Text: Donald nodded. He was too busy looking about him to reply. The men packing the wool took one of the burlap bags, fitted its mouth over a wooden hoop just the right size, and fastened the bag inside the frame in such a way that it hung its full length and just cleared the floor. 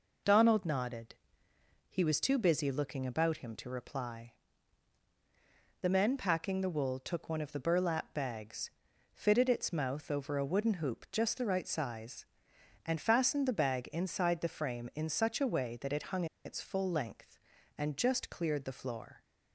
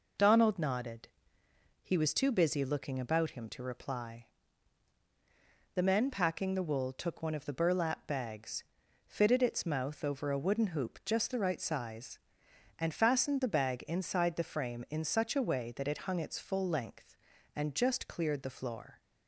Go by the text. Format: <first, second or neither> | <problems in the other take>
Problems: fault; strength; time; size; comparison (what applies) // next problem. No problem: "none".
second | pauses between "hung" and "its"; slight; at 16.2 s; 0.20 s long